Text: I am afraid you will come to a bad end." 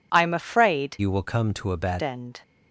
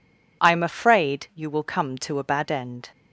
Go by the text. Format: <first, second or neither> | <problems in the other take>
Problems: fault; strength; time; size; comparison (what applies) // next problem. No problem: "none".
second | changes voice from "you" to "bad"; from 0.9 to 2.0 s; 1.1 s long